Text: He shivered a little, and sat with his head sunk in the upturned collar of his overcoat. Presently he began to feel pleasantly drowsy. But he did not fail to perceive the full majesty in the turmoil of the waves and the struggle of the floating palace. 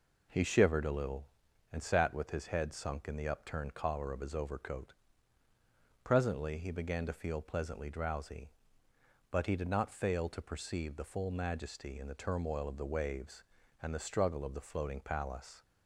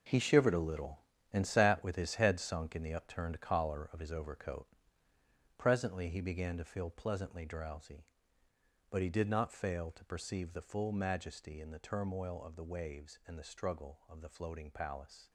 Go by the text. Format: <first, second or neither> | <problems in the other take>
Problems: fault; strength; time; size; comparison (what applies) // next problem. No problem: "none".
first | gets quieter; strong; throughout; 11 dB